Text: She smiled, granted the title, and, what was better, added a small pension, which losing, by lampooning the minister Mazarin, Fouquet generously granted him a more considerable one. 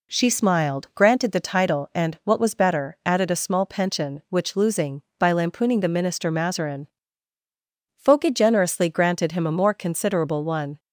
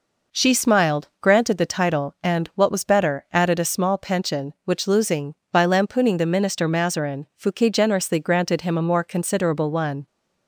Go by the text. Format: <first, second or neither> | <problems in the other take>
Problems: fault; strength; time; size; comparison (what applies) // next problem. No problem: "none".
neither | none